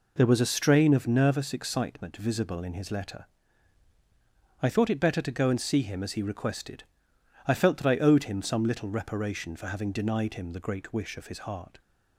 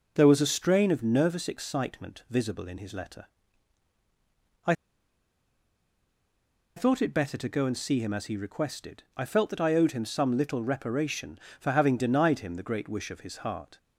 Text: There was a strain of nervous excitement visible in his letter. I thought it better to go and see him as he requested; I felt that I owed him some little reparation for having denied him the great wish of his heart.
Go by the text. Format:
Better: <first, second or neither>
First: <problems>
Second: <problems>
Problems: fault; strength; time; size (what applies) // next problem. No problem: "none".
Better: first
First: none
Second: pauses between "I" and "thought"; strong; at 4.7 s; 2.0 s long